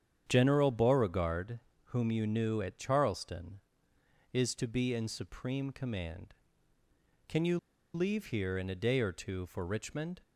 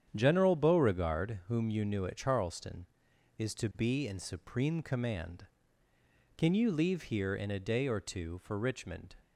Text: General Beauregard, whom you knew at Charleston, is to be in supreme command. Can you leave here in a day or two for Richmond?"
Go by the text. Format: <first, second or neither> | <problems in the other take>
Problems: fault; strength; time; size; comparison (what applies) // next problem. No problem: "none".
second | starts louder than the rest; strong; until 1.2 s; 8.5 dB; strong in the second // pauses between "you" and "leave"; at 7.5 s; 0.36 s long